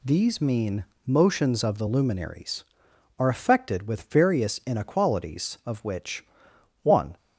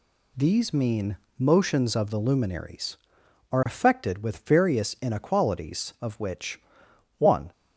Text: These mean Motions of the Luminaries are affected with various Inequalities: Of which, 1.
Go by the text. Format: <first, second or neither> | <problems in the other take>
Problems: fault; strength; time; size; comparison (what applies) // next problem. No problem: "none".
neither | pauses between "mean" and "Motions"; slight; the same in both